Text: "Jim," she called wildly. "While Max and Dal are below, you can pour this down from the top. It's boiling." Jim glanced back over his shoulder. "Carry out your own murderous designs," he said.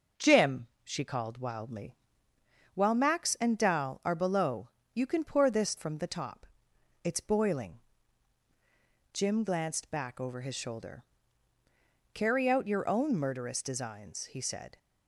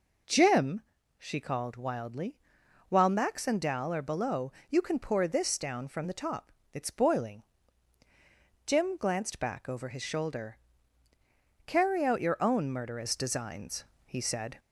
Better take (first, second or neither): second